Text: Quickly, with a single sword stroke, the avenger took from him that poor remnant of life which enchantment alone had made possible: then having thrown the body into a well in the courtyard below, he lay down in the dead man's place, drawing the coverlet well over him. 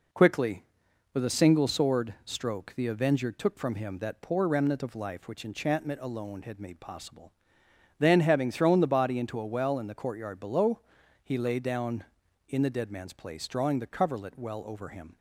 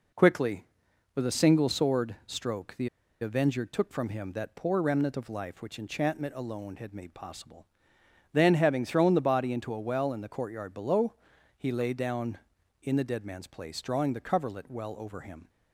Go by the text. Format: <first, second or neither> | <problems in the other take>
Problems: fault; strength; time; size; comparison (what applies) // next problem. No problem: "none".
first | pauses between "the" and "avenger"; slight; at 2.8 s; 0.32 s long